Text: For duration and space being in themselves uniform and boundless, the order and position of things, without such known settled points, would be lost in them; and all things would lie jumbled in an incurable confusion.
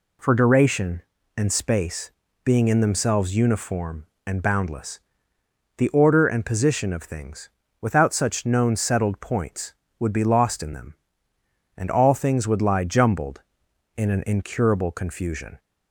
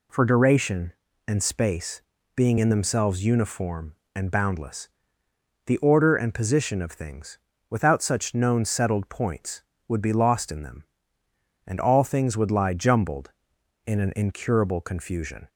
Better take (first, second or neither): neither